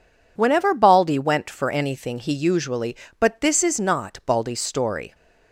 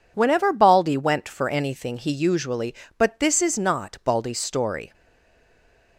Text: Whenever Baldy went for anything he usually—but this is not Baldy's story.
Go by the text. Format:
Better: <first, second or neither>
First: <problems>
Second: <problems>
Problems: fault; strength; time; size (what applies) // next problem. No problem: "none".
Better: first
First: none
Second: stays silent after the last word; from 4.9 s on; 1.0 s long